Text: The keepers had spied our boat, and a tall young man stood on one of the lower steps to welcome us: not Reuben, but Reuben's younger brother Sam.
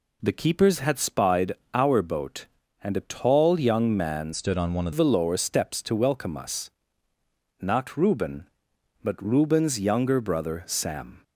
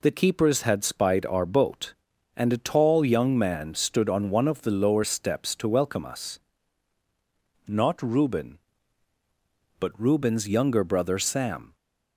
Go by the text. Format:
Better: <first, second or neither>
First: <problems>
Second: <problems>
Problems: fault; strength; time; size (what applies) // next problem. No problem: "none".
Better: second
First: pauses between "spied" and "our"; slight; at 1.5 s; 0.20 s long // changes voice from "stood" to "of"; from 4.3 to 4.9 s; 0.6 s long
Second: none